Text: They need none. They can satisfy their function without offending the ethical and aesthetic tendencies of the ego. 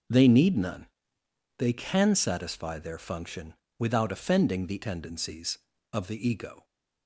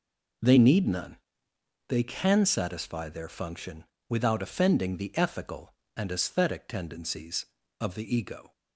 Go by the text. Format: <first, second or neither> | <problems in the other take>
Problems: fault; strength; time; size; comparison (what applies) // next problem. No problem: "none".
second | starts louder than the rest; until 1.8 s; 6 dB // pauses between "function" and "without"; slight; at 3.5 s; 0.24 s long; slight in the second // skips "ethical and aesthetic"; at 4.8 s